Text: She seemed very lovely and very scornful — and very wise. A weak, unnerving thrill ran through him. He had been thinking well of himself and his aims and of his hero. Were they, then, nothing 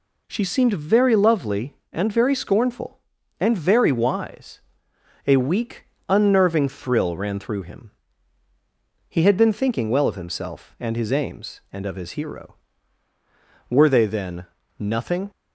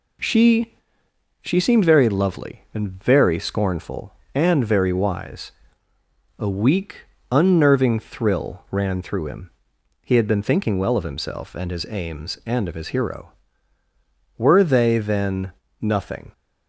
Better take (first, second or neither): first